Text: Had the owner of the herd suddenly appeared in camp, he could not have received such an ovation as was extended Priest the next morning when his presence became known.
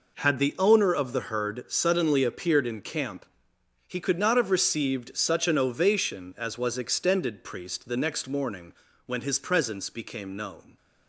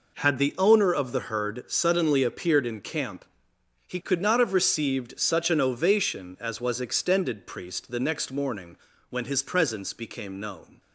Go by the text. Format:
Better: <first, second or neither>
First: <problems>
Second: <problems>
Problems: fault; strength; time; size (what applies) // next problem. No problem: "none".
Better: neither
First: pauses between "morning" and "when"; slight; at 8.7 s; 0.34 s long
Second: pauses between "morning" and "when"; slight; at 8.7 s; 0.34 s long